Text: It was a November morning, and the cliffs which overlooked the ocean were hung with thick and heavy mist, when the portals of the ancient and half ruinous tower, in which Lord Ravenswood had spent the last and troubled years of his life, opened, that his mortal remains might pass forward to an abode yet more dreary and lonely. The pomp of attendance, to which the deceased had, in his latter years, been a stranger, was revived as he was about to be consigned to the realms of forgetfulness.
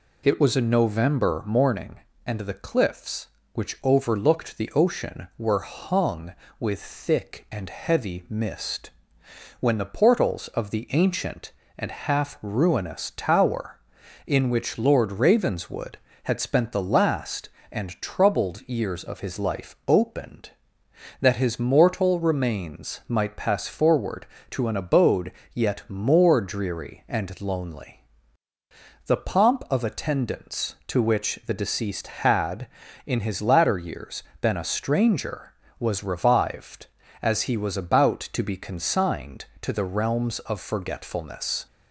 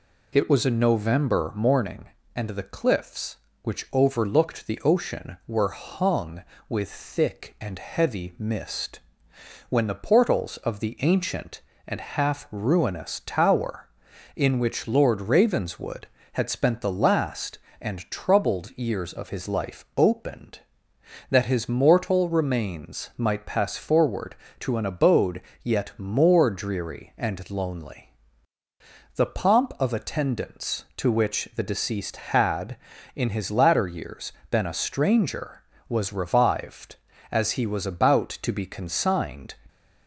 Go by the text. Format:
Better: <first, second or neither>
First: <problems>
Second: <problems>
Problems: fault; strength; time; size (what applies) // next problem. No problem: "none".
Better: first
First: pauses between "abode" and "yet"; slight; at 25.3 s; 0.20 s long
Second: pauses between "abode" and "yet"; slight; at 25.4 s; 0.20 s long // stops before "to the realms of forgetfulness"; at 39.6 s